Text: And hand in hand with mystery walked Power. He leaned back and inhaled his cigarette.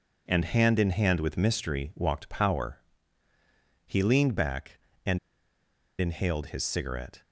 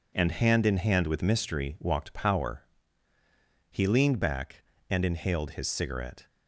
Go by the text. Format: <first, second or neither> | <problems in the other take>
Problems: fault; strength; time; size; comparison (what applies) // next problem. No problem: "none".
second | pauses between "and" and "inhaled"; noticeable; at 5.1 s; 0.81 s long